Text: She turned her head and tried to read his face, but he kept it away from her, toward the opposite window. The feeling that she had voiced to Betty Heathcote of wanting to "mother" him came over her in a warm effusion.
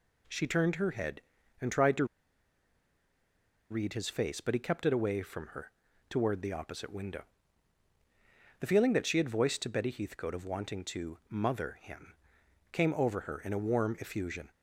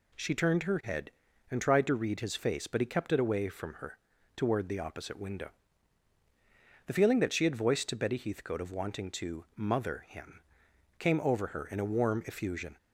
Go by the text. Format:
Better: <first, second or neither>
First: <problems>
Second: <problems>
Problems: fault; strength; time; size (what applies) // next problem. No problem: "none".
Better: second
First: pauses between "to" and "read"; strong; at 2.0 s; 1.6 s long // pauses between "him" and "came"; noticeable; at 12.1 s; 0.58 s long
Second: pauses between "him" and "came"; noticeable; at 10.4 s; 0.58 s long